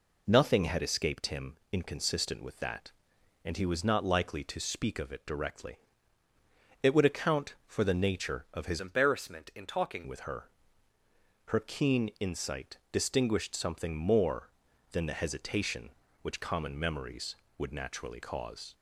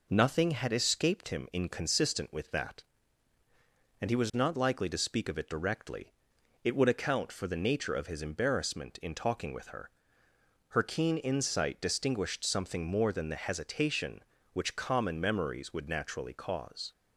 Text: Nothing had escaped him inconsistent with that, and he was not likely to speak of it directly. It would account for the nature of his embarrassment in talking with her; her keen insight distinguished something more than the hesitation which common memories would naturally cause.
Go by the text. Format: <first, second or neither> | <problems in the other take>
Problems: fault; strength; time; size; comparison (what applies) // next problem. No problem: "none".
second | pauses between "him" and "inconsistent"; slight; at 1.5 s; 0.16 s long // changes voice from "embarrassment" to "talking"; from 8.7 to 10.0 s; 1.3 s long